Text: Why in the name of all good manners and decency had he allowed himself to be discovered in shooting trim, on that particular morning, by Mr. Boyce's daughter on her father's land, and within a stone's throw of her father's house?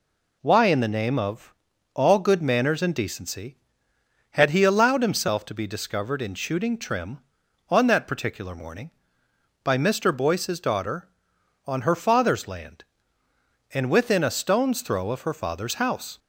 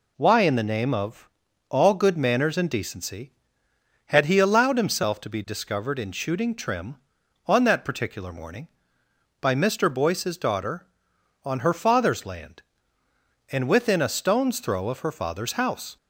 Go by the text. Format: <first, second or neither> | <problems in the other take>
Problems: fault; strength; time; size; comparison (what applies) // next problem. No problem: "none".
neither | pauses between "of" and "all"; the same in both